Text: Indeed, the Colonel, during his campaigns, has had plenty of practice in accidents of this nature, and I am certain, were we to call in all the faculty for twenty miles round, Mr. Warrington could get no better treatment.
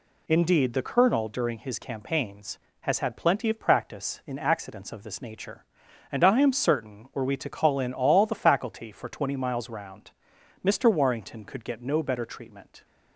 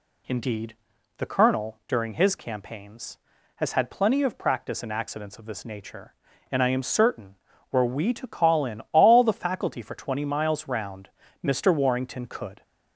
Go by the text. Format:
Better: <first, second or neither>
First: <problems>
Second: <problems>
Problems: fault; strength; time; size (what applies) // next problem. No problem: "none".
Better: first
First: none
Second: stops before "get no better treatment"; at 12.6 s